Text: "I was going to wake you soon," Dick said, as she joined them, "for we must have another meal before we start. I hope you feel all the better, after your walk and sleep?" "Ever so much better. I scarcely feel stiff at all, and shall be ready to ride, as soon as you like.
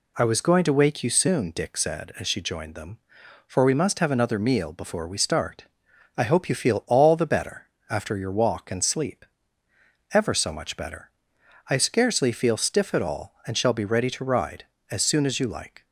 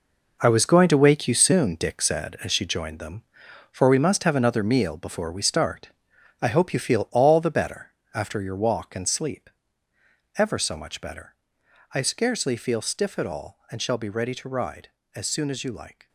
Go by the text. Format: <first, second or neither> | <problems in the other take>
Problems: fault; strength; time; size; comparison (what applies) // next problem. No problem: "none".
first | gets quieter; strong; throughout; 10.5 dB